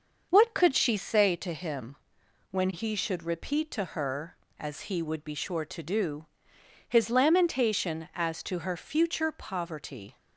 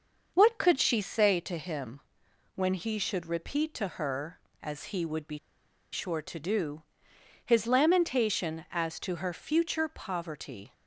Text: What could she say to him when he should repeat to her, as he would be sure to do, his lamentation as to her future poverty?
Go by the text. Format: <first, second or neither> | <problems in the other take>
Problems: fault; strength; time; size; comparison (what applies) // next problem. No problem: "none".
first | starts louder than the rest; until 1.3 s; 6.5 dB; also in the first // pauses between "him" and "when"; noticeable; at 2.0 s; 0.54 s long; noticeable in the first // pauses between "be" and "sure"; noticeable; at 5.3 s; 0.55 s long